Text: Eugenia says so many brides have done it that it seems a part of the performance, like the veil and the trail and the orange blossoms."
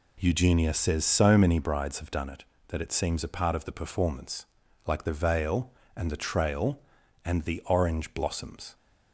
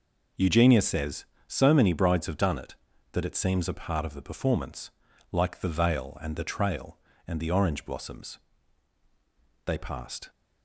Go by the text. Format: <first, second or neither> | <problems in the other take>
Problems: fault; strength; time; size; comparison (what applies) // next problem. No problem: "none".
first | goes on to say "They passed"; noticeable; from 9.6 s on; 0.64 s long